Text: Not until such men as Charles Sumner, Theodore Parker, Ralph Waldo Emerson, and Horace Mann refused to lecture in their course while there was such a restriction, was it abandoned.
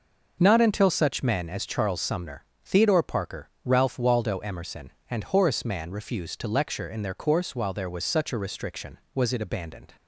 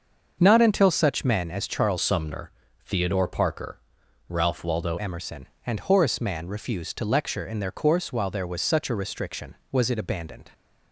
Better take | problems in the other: first | starts louder than the rest; until 1.4 s; 6.5 dB // changes voice from "Sumner" to "Waldo"; from 2.0 to 4.9 s; 2.9 s long

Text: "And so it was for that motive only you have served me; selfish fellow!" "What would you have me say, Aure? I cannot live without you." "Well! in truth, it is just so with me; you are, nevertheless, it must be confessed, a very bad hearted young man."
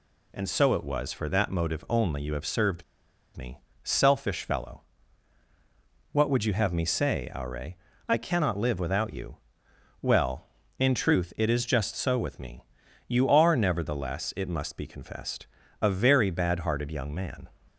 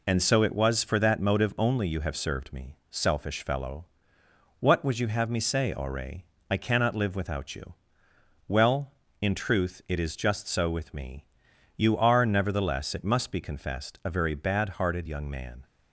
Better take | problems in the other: second | pauses between "served" and "me"; noticeable; at 2.8 s; 0.52 s long

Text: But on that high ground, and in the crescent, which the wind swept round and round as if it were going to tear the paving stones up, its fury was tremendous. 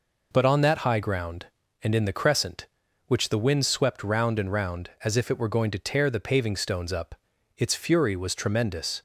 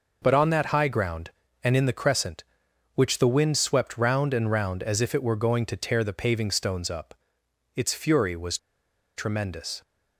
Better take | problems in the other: first | pauses between "was" and "tremendous"; noticeable; at 8.5 s; 0.59 s long

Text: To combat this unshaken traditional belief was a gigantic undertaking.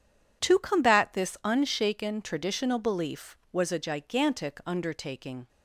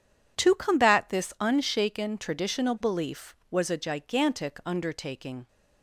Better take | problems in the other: neither | none

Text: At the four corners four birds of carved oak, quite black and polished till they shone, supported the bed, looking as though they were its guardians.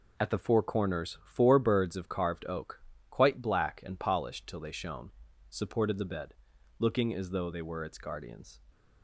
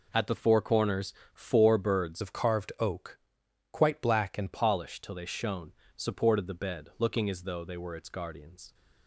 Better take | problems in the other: first | pauses between "corners" and "four"; slight; at 1.1 s; 0.20 s long // changes voice from "of" to "and"; from 2.2 to 4.5 s; 2.3 s long

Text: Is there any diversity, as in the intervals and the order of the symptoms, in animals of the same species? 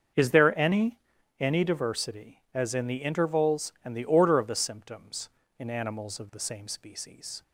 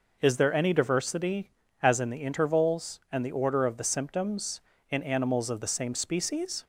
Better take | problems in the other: second | starts louder than the rest; until 1.5 s; 6.5 dB // says "any" twice; at 1.3 s

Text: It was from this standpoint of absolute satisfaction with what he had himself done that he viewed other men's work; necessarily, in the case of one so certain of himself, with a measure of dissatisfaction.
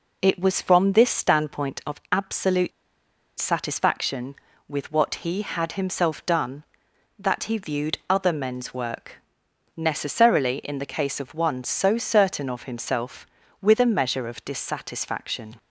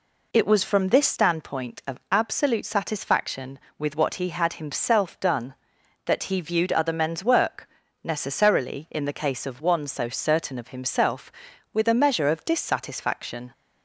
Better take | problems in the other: second | pauses between "absolute" and "satisfaction"; noticeable; at 2.7 s; 0.69 s long

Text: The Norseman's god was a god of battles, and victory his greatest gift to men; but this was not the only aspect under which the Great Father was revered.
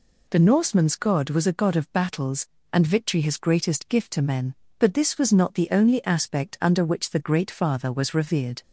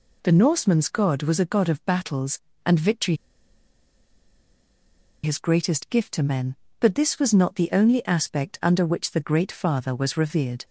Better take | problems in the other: first | pauses between "victory" and "his"; strong; at 3.1 s; 2.0 s long

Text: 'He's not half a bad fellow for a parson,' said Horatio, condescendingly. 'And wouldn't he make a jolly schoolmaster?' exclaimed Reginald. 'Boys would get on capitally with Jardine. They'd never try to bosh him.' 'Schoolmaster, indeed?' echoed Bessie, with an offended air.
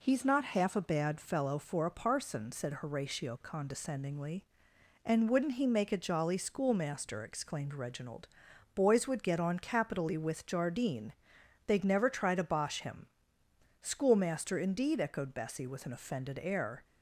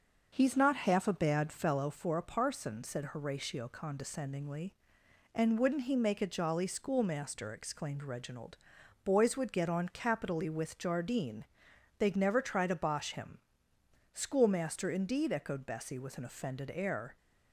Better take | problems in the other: first | starts louder than the rest; noticeable; until 1.9 s; 6 dB

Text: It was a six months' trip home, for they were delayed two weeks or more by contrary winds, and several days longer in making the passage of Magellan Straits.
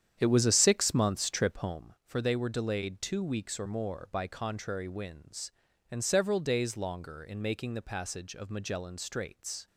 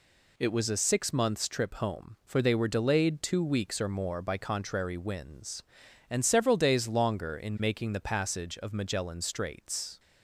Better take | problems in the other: second | starts louder than the rest; strong; until 1.8 s; 9 dB

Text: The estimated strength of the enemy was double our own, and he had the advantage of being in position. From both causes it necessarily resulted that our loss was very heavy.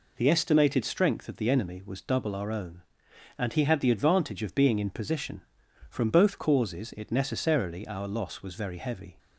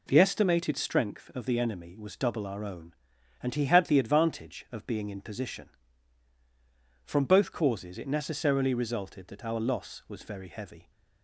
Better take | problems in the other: second | skips "resulted that"; at 7.8 s

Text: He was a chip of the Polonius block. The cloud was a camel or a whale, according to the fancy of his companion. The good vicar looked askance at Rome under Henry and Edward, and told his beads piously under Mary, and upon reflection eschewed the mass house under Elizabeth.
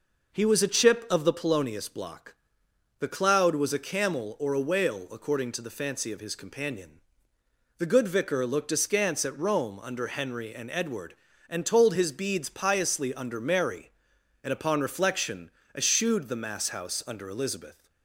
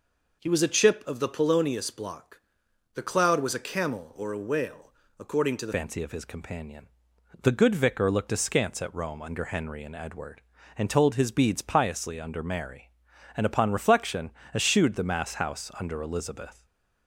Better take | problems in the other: first | changes voice at "fancy"; from 5.7 s on; 10.9 s long // pauses between "reflection" and "eschewed"; slight; at 14.3 s; 0.22 s long; slight in the first // stays silent after the last word; slight; from 16.5 s on; 0.5 s long

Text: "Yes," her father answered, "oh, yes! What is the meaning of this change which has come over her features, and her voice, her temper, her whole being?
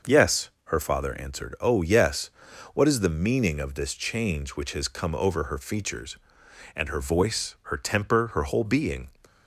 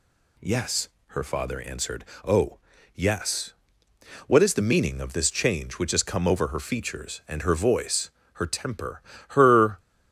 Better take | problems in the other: first | stops before "whole being"; at 9.7 s

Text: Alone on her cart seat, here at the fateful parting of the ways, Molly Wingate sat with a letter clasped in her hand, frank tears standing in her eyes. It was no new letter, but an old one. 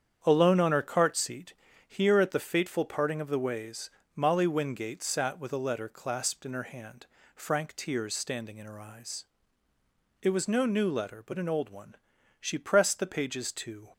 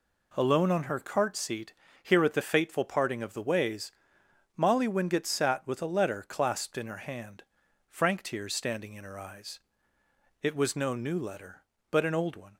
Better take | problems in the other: second | starts louder than the rest; strong; until 1.2 s; 8.5 dB // goes on to say "She pressed the pages to"; from 12.3 s on; 1.5 s long

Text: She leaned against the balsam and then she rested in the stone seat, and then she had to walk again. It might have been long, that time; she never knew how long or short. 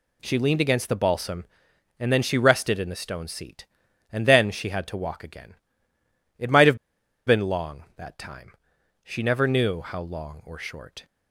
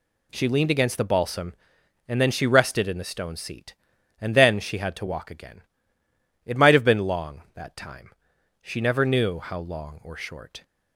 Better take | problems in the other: second | pauses between "have" and "been"; noticeable; at 6.7 s; 0.50 s long

